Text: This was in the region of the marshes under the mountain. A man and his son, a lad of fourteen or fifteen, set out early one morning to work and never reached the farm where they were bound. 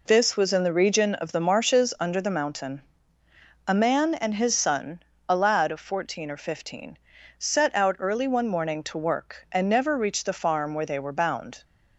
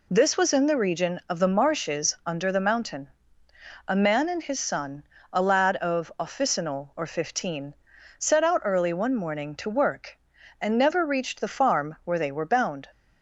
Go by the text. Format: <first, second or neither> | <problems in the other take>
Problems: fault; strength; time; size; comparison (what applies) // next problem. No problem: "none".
first | says "officinal" for "fourteen"; at 6.1 s